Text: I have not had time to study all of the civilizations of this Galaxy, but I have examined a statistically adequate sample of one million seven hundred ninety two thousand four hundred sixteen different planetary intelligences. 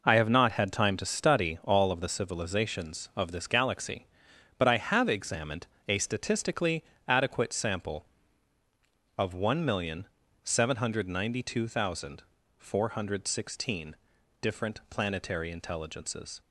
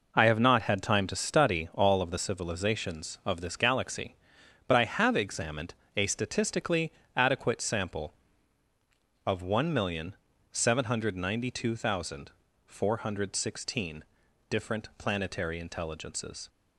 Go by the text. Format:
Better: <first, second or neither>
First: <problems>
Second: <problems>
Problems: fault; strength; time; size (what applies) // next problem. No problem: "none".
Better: neither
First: pauses between "examined" and "a"; slight; at 5.6 s; 0.21 s long // pauses between "statistically" and "adequate"; slight; at 6.8 s; 0.24 s long // pauses between "million" and "seven"; slight; at 10.0 s; 0.36 s long // pauses between "thousand" and "four"; slight; at 12.2 s; 0.34 s long // pauses between "sixteen" and "different"; noticeable; at 13.9 s; 0.46 s long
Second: pauses between "examined" and "a"; slight; at 5.7 s; 0.22 s long // pauses between "statistically" and "adequate"; slight; at 6.9 s; 0.24 s long // pauses between "million" and "seven"; slight; at 10.1 s; 0.36 s long // pauses between "thousand" and "four"; slight; at 12.3 s; 0.34 s long // pauses between "sixteen" and "different"; noticeable; at 14.0 s; 0.46 s long